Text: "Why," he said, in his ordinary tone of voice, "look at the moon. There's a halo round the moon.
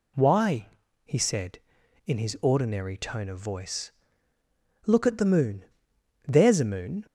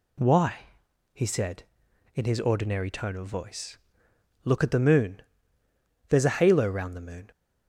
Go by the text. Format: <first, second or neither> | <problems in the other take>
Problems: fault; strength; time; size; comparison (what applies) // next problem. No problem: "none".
second | skips "halo round the"; at 6.6 s